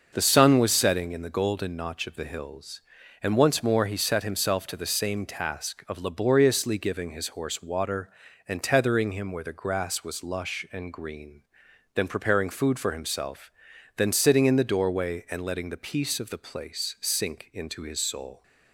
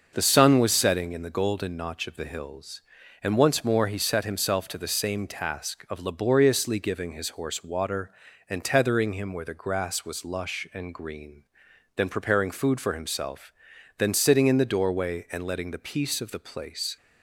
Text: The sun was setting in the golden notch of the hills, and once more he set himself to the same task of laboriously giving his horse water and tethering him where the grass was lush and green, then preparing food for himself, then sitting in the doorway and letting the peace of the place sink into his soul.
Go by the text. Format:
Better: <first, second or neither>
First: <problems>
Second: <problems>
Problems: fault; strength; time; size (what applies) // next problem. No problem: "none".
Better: first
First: starts louder than the rest; until 1.1 s; 6 dB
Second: starts louder than the rest; until 1.1 s; 6 dB // stops before "sink into his soul"; at 16.9 s